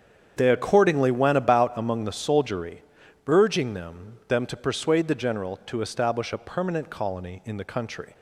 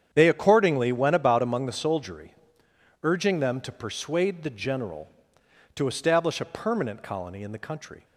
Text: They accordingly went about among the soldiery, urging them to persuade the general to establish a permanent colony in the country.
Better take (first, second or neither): second